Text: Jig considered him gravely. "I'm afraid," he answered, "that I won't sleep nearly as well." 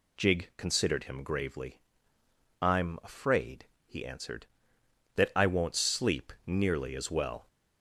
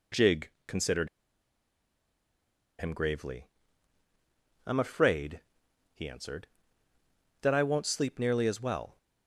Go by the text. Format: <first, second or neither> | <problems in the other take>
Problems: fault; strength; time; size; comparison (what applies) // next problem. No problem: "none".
first | pauses between "Jig" and "considered"; slight; at 0.5 s; 0.16 s long // pauses between "considered" and "him"; strong; at 1.0 s; 1.7 s long